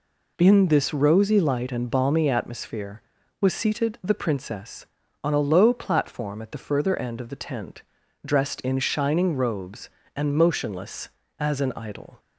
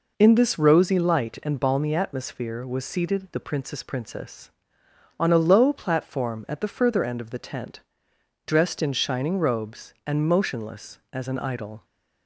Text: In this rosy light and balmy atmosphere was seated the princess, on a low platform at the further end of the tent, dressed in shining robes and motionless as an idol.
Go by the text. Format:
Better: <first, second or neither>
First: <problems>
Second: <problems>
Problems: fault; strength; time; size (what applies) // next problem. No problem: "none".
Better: first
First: none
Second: says "princess" twice; at 3.8 s